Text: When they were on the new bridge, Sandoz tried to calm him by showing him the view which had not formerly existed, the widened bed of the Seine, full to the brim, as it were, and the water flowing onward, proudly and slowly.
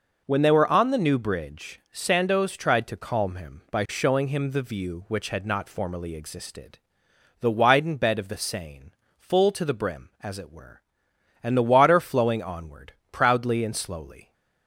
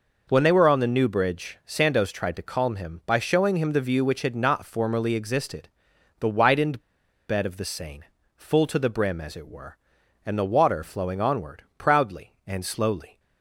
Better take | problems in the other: first | pauses between "widened" and "bed"; noticeable; at 6.8 s; 0.46 s long

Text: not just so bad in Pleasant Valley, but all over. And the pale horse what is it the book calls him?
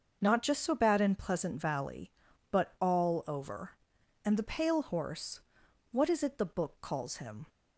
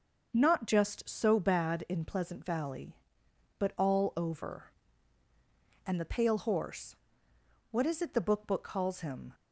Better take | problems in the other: first | starts louder than the rest; noticeable; until 1.3 s; 6 dB; also in the first // pauses between "horse" and "what"; noticeable; at 6.9 s; 0.76 s long; noticeable in the first // says "book" twice; at 8.4 s

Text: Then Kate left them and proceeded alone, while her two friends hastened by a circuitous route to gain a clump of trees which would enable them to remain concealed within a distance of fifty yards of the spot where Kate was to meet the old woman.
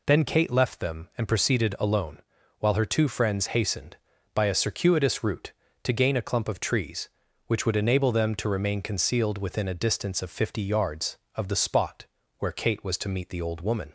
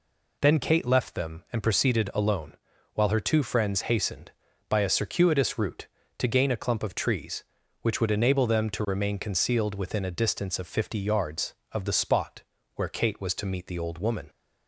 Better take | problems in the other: neither | pauses between "spot" and "where"; slight; the same in both

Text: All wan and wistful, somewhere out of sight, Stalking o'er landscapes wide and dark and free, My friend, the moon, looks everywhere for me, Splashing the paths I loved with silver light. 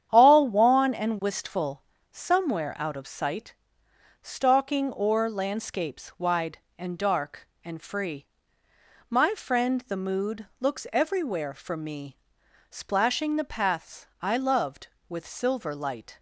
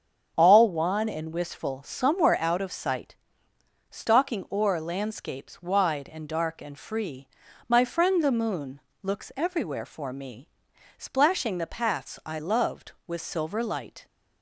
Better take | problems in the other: second | starts louder than the rest; strong; until 1.1 s; 9.5 dB; strong in the second // says "mood" for "moon"; at 9.9 s // pauses between "paths" and "I"; slight; at 14.0 s; 0.16 s long

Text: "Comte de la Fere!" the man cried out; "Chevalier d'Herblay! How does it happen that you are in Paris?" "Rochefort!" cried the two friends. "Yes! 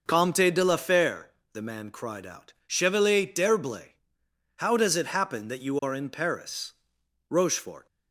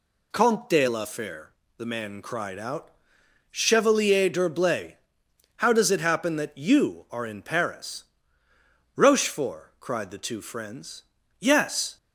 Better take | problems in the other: second | stops before "cried the two friends Yes"; at 7.8 s

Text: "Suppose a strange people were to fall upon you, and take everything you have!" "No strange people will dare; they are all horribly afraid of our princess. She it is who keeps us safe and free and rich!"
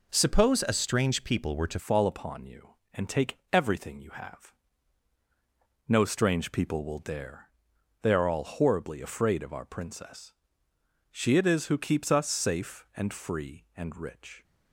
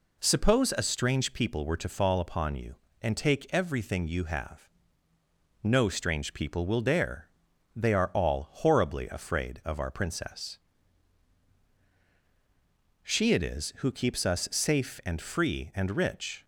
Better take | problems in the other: second | changes voice at "fall"; from 1.7 s on; 12.7 s long // pauses between "take" and "everything"; slight; at 3.3 s; 0.16 s long

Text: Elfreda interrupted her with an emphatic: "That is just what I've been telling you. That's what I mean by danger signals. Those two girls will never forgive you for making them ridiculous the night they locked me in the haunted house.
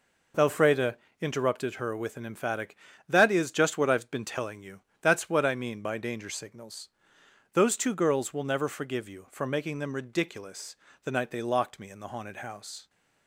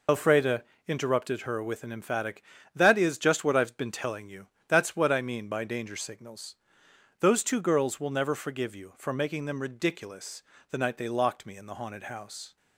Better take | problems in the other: first | loses the start of "Elfreda"; at 0.0 s; 75 ms // pauses between "Elfreda" and "interrupted"; slight; at 0.6 s; 0.24 s long; slight in the first // pauses between "ridiculous" and "the"; slight; at 10.4 s; 0.28 s long; slight in the first

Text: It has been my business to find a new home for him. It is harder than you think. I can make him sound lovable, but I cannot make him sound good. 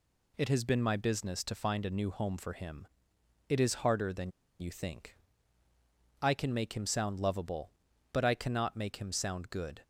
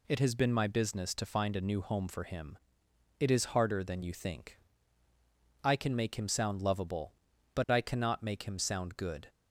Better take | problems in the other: second | pauses between "than" and "you"; slight; at 4.3 s; 0.30 s long

